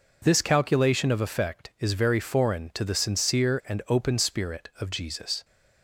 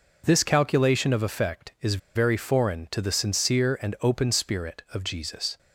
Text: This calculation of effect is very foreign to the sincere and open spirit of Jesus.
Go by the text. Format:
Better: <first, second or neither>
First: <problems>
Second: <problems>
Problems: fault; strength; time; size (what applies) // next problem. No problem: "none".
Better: first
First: none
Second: pauses between "is" and "very"; slight; at 1.9 s; 0.15 s long